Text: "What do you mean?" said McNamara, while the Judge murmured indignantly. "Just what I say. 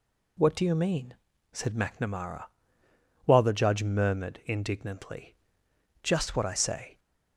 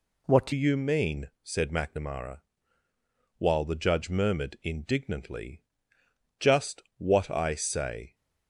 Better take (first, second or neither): first